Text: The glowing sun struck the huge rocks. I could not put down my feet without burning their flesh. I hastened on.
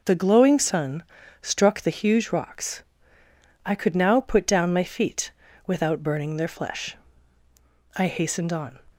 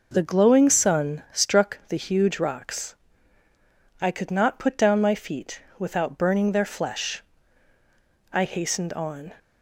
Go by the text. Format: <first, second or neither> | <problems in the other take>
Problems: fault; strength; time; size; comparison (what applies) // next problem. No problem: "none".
second | pauses between "sun" and "struck"; at 1.0 s; 0.40 s long // says "now" for "not"; at 3.9 s // pauses between "feet" and "without"; slight; at 5.3 s; 0.36 s long; slight in the second